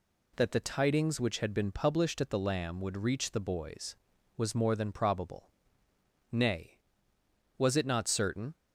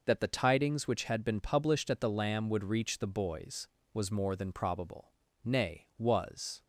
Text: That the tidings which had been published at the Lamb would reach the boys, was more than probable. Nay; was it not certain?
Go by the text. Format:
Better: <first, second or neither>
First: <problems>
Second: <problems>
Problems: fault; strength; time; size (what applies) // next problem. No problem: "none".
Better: first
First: none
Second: stops before "it not certain"; at 6.6 s